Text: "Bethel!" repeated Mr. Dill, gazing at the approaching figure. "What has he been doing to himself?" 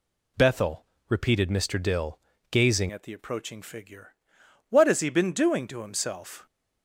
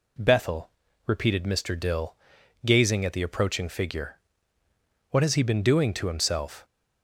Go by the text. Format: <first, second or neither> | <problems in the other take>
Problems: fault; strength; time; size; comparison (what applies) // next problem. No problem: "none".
second | changes voice at "at"; from 2.9 s on; 3.5 s long